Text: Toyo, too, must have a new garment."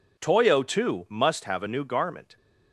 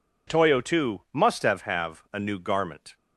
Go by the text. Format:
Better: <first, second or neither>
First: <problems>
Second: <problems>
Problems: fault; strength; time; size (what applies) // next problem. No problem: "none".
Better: first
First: none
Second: says "have" twice; at 1.6 s